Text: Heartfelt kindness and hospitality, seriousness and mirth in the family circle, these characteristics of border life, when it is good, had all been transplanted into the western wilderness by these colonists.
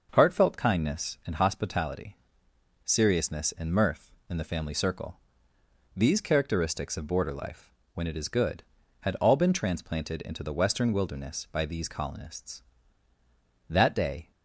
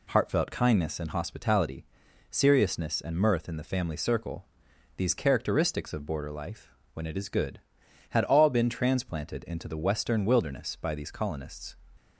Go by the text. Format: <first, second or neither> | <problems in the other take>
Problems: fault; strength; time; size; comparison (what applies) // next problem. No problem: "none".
second | starts louder than the rest; noticeable; until 1.1 s; 6 dB // goes on to say "That day"; noticeable; from 13.6 s on; 0.62 s long